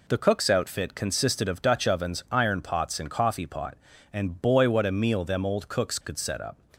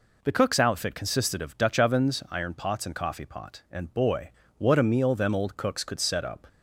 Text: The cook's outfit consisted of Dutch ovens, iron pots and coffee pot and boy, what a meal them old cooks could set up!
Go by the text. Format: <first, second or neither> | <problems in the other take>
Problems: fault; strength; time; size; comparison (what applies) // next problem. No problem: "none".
neither | none